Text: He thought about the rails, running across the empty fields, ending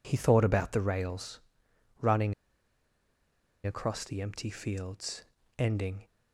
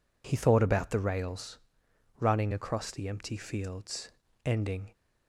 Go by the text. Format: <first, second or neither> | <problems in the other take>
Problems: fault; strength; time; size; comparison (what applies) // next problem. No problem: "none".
second | pauses between "running" and "across"; strong; at 2.3 s; 1.3 s long